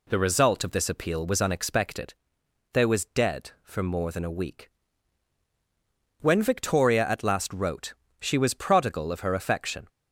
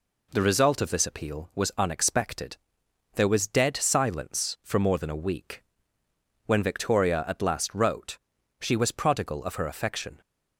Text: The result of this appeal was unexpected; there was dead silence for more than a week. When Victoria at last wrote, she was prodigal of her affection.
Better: second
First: skips "silence"; at 3.5 s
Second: none

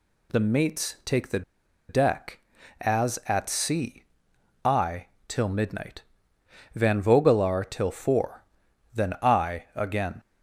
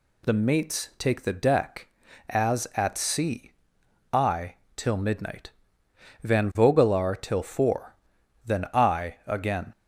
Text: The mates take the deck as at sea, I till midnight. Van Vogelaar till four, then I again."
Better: second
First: pauses between "the" and "deck"; noticeable; at 1.4 s; 0.48 s long // pauses between "I" and "till"; slight; at 5.0 s; 0.20 s long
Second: pauses between "I" and "till"; slight; at 4.5 s; 0.20 s long

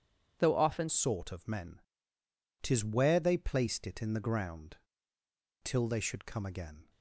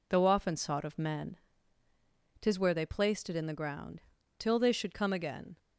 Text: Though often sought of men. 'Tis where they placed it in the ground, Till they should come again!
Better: second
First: changes voice at "sought"; from 0.8 s on; 6.0 s long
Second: none

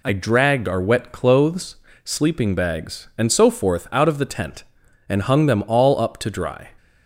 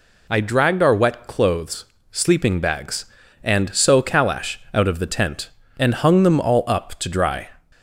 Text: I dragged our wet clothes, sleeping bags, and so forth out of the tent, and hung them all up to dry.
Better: first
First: none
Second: says "calash" for "forth"; at 4.0 s

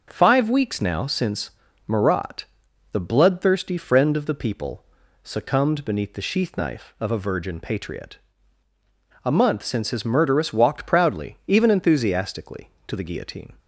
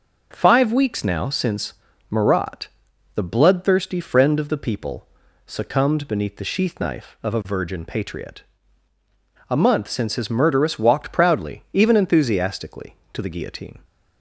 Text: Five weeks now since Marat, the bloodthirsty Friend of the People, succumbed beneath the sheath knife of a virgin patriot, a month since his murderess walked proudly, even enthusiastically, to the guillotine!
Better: neither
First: pauses between "since" and "Marat"; slight; at 1.5 s; 0.36 s long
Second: pauses between "since" and "Marat"; slight; at 1.7 s; 0.36 s long

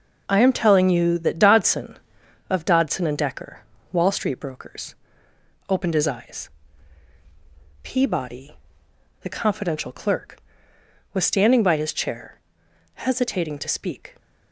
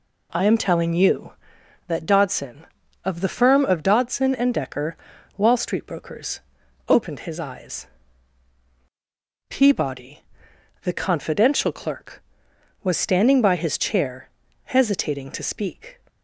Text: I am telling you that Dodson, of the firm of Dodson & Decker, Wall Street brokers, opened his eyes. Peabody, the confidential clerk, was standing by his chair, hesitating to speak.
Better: second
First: skips "the firm of"; at 2.6 s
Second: none

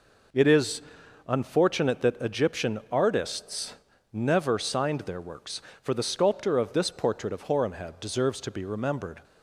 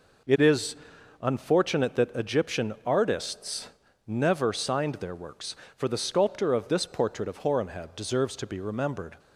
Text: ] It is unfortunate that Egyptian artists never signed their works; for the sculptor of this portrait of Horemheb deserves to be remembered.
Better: neither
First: pauses between "is" and "unfortunate"; noticeable; at 0.8 s; 0.46 s long // pauses between "artists" and "never"; at 3.7 s; 0.38 s long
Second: pauses between "is" and "unfortunate"; noticeable; at 0.7 s; 0.46 s long // pauses between "artists" and "never"; at 3.6 s; 0.38 s long

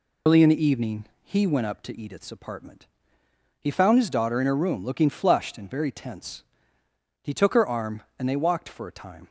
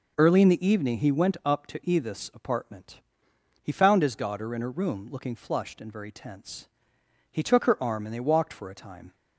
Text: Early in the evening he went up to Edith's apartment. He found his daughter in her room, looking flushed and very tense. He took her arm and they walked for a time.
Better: second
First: loses the start of "Early"; at 0.2 s; 95 ms // pauses between "evening" and "he"; slight; at 1.0 s; 0.16 s long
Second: none

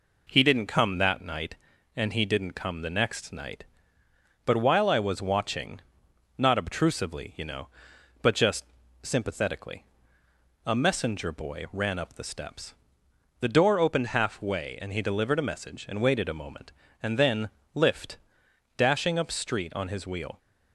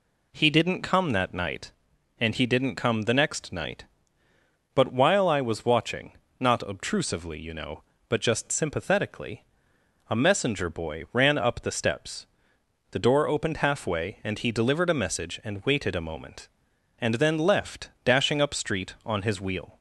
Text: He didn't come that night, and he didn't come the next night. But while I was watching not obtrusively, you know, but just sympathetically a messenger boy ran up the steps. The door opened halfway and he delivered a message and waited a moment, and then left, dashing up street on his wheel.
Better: second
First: pauses between "watching" and "not"; noticeable; at 5.7 s; 0.60 s long // pauses between "just" and "sympathetically"; at 8.6 s; 0.38 s long // pauses between "sympathetically" and "a"; noticeable; at 9.8 s; 0.82 s long // says "lift" for "left"; at 17.7 s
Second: pauses between "watching" and "not"; slight; at 6.1 s; 0.26 s long // pauses between "sympathetically" and "a"; noticeable; at 9.4 s; 0.64 s long

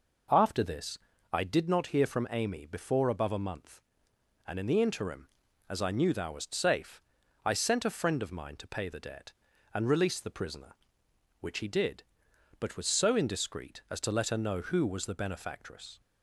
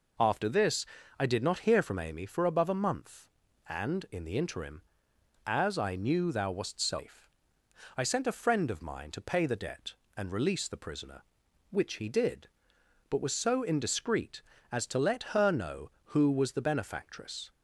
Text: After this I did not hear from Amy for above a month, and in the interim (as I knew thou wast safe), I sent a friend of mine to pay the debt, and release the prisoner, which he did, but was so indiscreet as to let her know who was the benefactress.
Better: second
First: pauses between "this" and "I"; slight; at 0.9 s; 0.34 s long // says "before" for "for"; at 2.6 s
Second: pauses between "this" and "I"; slight; at 0.8 s; 0.34 s long

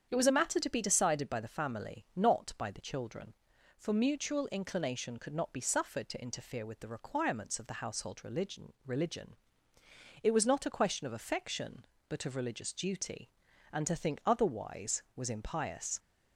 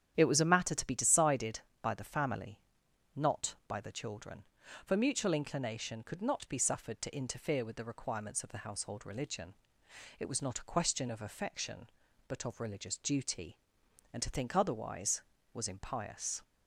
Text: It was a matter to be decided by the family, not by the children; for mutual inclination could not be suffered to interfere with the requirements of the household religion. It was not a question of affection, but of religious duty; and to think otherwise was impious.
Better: second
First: starts louder than the rest; strong; until 1.1 s; 8 dB // says "religion" twice; at 8.8 s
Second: starts louder than the rest; strong; until 1.1 s; 9.5 dB

